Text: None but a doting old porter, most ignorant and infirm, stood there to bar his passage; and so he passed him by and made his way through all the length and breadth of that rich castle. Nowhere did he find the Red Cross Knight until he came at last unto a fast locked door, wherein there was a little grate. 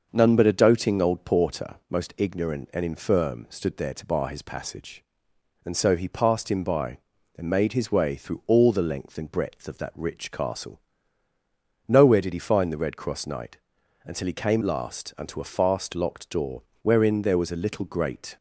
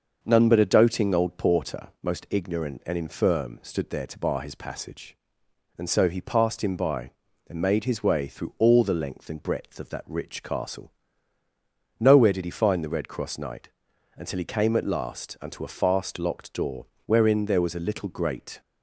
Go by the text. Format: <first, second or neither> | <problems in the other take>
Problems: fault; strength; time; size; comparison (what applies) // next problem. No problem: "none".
second | starts louder than the rest; noticeable; until 1.1 s; 6 dB; noticeable in the second // pauses between "Knight" and "until"; at 13.5 s; 0.44 s long; also in the second // skips "at"; at 14.6 s